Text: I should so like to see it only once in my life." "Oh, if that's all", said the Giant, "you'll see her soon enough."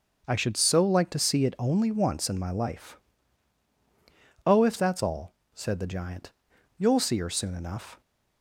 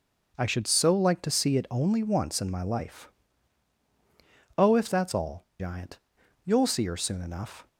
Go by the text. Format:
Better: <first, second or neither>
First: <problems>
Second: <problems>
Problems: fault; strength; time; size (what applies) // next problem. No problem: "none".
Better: first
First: none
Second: skips "said the"; at 5.5 s